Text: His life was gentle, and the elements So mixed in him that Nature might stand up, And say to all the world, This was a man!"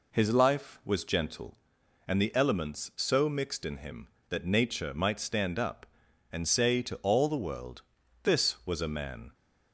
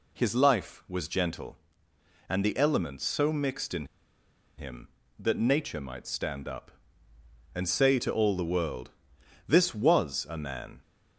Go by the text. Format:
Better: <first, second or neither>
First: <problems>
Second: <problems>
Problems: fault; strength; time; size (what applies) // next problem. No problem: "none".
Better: first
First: none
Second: pauses between "in" and "him"; noticeable; at 3.8 s; 0.73 s long